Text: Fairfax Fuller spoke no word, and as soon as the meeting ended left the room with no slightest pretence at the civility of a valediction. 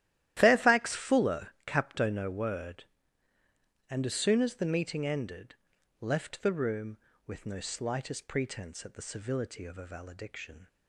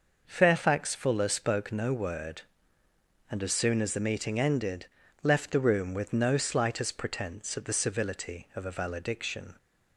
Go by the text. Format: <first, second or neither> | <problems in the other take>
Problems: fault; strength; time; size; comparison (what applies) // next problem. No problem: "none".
second | starts louder than the rest; strong; until 1.4 s; 13 dB // says "capto" for "spoke"; at 1.6 s // pauses between "ended" and "left"; at 5.5 s; 0.43 s long; slight in the second